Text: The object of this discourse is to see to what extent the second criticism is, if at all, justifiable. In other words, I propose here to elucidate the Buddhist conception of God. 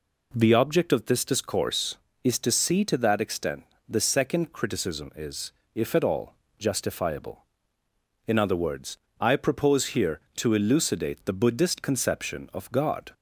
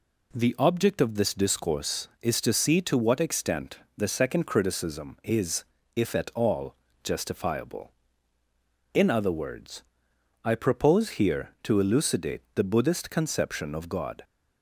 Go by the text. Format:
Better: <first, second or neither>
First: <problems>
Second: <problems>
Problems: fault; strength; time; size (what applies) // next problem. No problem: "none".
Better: second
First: says "that" for "what"; at 2.9 s // pauses between "extent" and "the"; slight; at 3.6 s; 0.22 s long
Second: pauses between "extent" and "the"; slight; at 3.7 s; 0.18 s long